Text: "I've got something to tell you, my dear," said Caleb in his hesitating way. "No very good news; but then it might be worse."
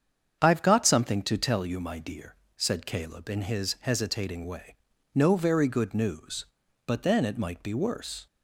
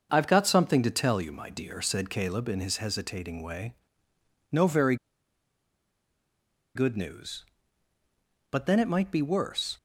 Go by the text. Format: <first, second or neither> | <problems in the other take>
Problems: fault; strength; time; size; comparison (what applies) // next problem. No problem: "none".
first | starts louder than the rest; until 1.1 s; 6 dB; strong in the first // pauses between "very" and "good"; strong; at 4.9 s; 1.7 s long